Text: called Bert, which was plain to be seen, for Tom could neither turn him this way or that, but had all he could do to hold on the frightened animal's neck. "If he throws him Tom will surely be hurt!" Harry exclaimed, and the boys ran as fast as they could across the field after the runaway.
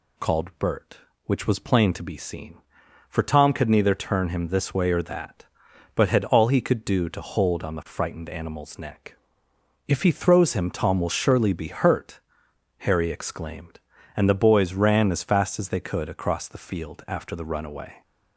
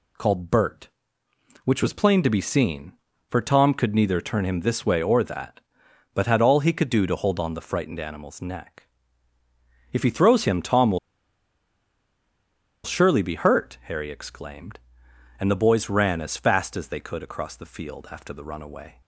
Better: first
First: none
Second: pauses between "will" and "surely"; strong; at 10.9 s; 1.8 s long

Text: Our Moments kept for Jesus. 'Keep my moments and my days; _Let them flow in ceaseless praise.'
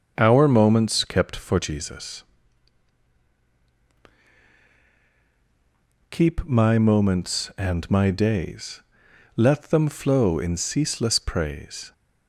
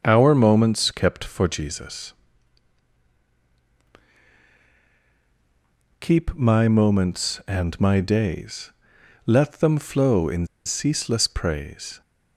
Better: first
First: starts louder than the rest; until 1.1 s; 6.5 dB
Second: starts louder than the rest; until 1.0 s; 6.5 dB // pauses between "in" and "ceaseless"; slight; at 10.4 s; 0.19 s long

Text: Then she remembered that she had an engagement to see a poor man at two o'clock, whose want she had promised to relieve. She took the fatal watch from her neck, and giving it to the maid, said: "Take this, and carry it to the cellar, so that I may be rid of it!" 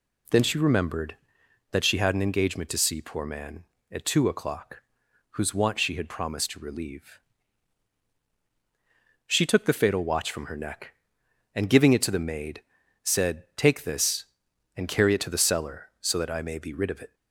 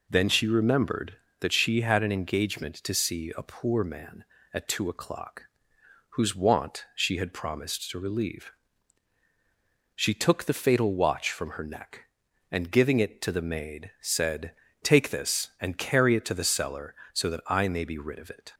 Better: second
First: skips "a"; at 3.0 s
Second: none

